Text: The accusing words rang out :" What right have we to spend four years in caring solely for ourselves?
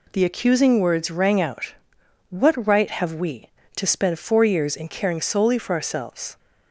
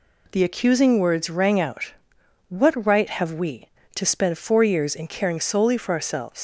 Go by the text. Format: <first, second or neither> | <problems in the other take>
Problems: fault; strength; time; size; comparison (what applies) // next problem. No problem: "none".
first | leaves "ourselves" unfinished; at 6.3 s; 135 ms